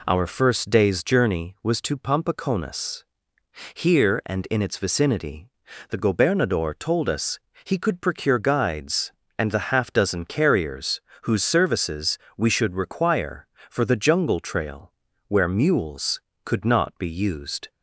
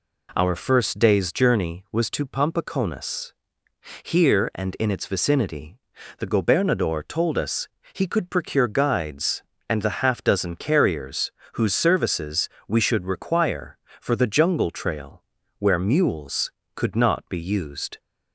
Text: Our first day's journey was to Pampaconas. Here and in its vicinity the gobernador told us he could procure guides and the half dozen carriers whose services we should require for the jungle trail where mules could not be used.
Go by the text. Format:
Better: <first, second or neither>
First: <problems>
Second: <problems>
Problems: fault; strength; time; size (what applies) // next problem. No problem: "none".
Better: neither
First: pauses between "vicinity" and "the"; at 5.4 s; 0.42 s long // pauses between "us" and "he"; slight; at 7.3 s; 0.24 s long // pauses between "carriers" and "whose"; slight; at 11.0 s; 0.22 s long // pauses between "services" and "we"; slight; at 12.1 s; 0.20 s long // pauses between "trail" and "where"; slight; at 14.9 s; 0.36 s long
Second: pauses between "vicinity" and "the"; at 5.7 s; 0.42 s long // pauses between "us" and "he"; slight; at 7.6 s; 0.24 s long // pauses between "carriers" and "whose"; slight; at 11.3 s; 0.22 s long // pauses between "services" and "we"; slight; at 12.4 s; 0.20 s long // pauses between "trail" and "where"; slight; at 15.2 s; 0.36 s long